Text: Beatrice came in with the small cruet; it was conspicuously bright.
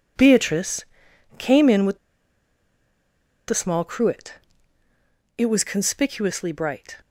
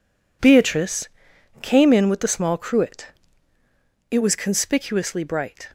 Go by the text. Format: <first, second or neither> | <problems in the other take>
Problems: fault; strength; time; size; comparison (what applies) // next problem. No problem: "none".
second | pauses between "Beatrice" and "came"; noticeable; at 0.8 s; 0.54 s long; noticeable in the second // pauses between "with" and "the"; strong; at 1.9 s; 1.4 s long